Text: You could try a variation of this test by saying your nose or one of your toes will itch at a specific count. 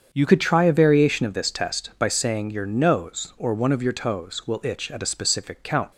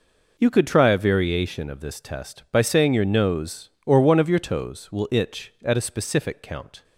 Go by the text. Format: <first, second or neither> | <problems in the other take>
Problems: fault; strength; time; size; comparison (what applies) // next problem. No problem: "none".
second | starts louder than the rest; strong; until 1.1 s; 7.5 dB // changes voice at "could"; from 0.2 s on; 5.7 s long